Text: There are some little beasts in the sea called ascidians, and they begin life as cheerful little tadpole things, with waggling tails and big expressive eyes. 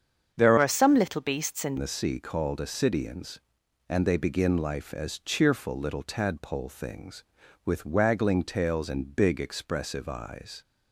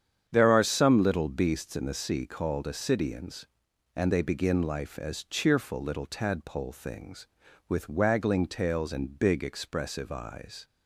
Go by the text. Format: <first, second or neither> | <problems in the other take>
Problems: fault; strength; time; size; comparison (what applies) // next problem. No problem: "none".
second | starts louder than the rest; strong; until 1.3 s; 7.5 dB; strong in the second // changes voice from "are" to "in"; from 0.5 to 1.7 s; 1.2 s long